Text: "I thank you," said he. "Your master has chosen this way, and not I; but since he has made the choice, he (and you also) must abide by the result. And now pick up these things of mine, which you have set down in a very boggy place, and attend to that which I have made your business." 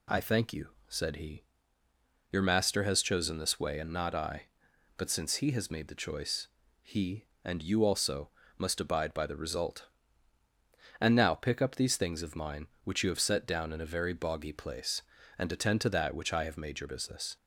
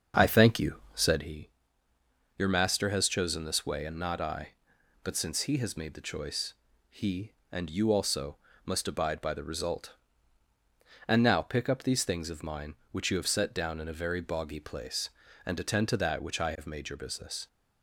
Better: first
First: none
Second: starts louder than the rest; until 1.2 s; 7 dB

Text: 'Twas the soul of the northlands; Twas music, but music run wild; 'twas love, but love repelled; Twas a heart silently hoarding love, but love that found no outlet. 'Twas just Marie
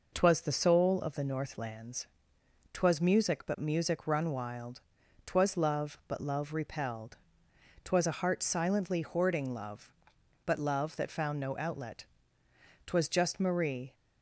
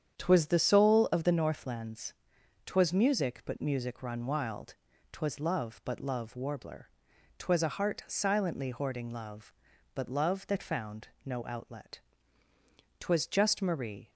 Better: first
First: none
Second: starts louder than the rest; strong; until 1.2 s; 8.5 dB // says "warbler" for "repelled"; at 6.3 s // pauses between "found" and "no"; slight; at 11.0 s; 0.16 s long

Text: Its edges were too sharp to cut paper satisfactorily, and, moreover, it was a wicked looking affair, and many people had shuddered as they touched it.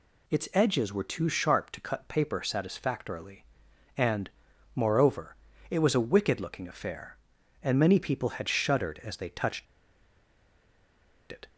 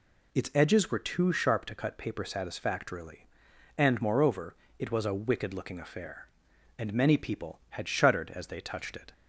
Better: second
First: pauses between "touched" and "it"; strong; at 9.6 s; 1.6 s long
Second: none

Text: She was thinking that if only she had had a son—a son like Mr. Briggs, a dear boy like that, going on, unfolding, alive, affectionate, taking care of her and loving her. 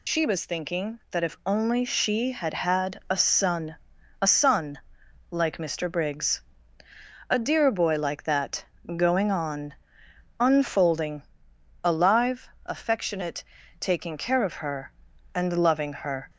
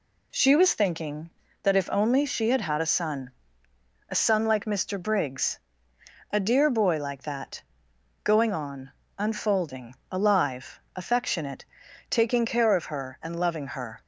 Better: second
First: loses the start of "She"; at 0.0 s; 50 ms // pauses between "son" and "like"; noticeable; at 4.7 s; 0.54 s long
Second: none

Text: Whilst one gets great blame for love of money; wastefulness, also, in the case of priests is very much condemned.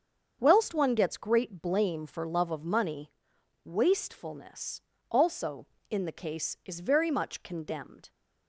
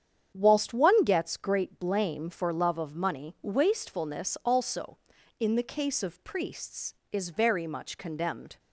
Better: second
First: starts louder than the rest; until 1.4 s; 7 dB // skips "of priests"; at 6.5 s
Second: starts louder than the rest; strong; until 1.3 s; 8.5 dB

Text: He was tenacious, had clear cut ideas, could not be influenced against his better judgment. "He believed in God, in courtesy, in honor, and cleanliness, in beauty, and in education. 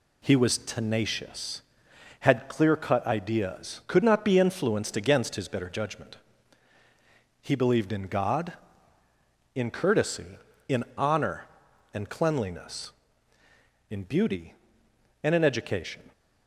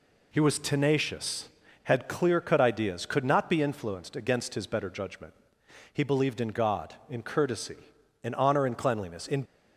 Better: first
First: none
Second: stops before "beauty and in education"; at 9.4 s

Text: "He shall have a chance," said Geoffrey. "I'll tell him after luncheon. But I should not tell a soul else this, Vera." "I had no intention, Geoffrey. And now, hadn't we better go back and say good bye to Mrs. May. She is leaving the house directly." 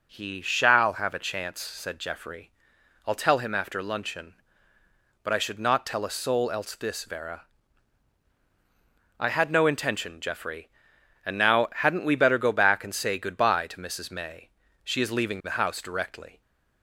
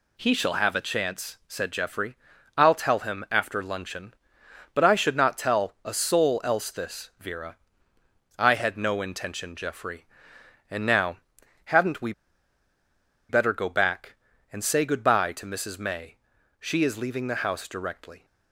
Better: first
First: none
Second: pauses between "we" and "better"; at 12.1 s; 1.1 s long

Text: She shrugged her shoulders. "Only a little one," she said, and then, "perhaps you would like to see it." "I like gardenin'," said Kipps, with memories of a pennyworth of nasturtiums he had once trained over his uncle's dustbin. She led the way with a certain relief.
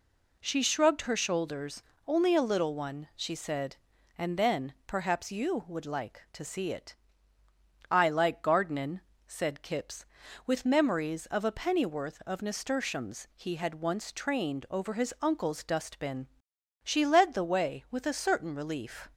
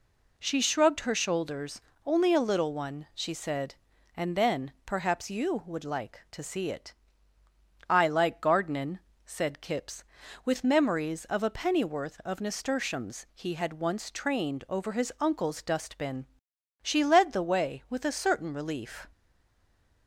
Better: first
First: none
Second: stays silent after the last word; slight; from 19.1 s on; 0.9 s long

